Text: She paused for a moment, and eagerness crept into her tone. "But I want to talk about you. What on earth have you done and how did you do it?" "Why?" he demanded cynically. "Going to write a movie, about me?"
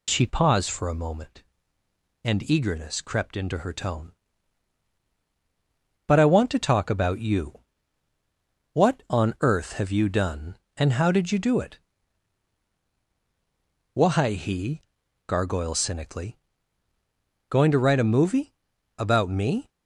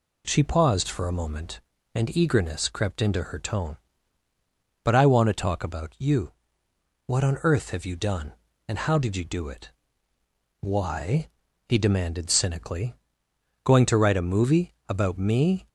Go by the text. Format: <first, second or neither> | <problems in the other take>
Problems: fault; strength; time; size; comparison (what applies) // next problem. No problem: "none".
second | says "gargoyle" for "demanded"; at 15.2 s